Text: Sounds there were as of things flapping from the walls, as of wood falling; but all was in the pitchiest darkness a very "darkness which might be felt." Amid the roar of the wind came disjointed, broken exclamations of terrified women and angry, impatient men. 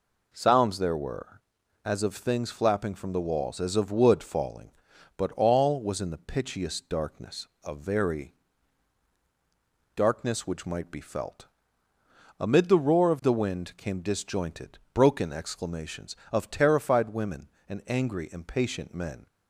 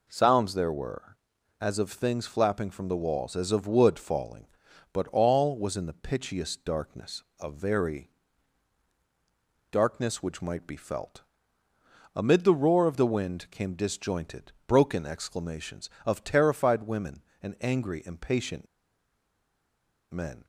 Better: first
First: pauses between "darkness" and "a"; slight; at 7.4 s; 0.20 s long // pauses between "very" and "darkness"; strong; at 8.3 s; 1.6 s long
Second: pauses between "darkness" and "a"; slight; at 7.2 s; 0.20 s long // pauses between "very" and "darkness"; strong; at 8.1 s; 1.6 s long // pauses between "impatient" and "men"; strong; at 18.6 s; 1.4 s long

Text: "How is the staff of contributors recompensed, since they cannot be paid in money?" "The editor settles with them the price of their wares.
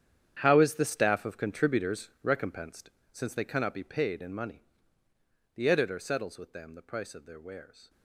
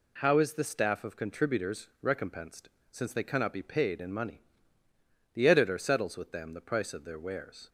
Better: second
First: gets quieter; strong; throughout; 14.5 dB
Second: none

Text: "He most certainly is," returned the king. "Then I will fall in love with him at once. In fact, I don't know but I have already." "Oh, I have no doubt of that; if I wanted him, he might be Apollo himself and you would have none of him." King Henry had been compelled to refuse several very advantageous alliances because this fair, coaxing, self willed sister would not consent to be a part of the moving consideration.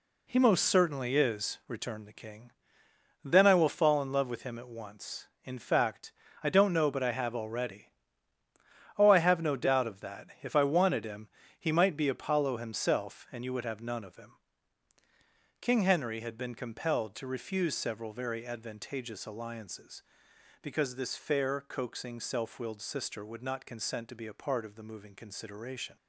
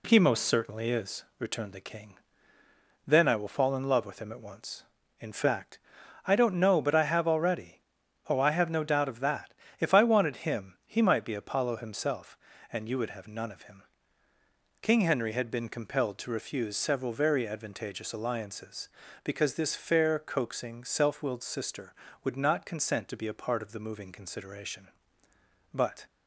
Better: first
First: none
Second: goes on to say "But"; slight; from 25.7 s on; 0.30 s long

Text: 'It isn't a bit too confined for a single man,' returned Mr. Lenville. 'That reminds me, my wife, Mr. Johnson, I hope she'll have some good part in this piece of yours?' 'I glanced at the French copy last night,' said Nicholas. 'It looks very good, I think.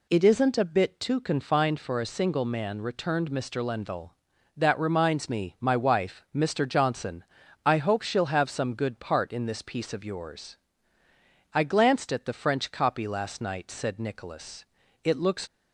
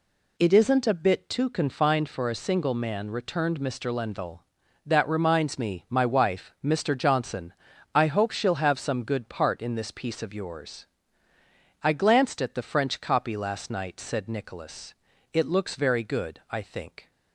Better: second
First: stops before "very good I think"; at 15.4 s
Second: none

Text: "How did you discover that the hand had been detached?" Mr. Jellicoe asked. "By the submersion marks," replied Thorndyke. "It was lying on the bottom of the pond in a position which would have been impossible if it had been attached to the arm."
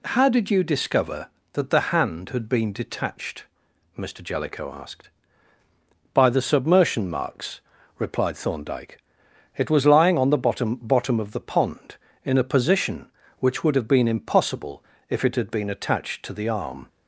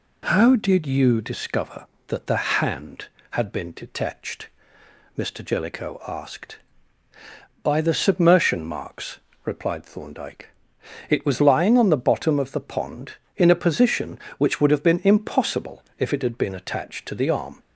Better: second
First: says "bottom" twice; at 10.7 s // pauses between "impossible" and "if"; slight; at 14.8 s; 0.24 s long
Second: pauses between "impossible" and "if"; slight; at 15.8 s; 0.16 s long

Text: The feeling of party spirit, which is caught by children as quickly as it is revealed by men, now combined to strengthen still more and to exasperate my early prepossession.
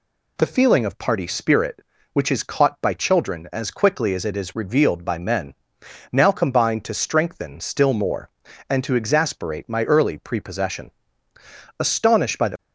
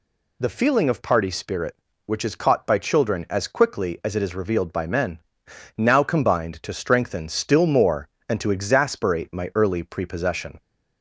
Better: second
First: goes on to say "Astonished by the"; noticeable; from 11.7 s on; 0.78 s long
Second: none

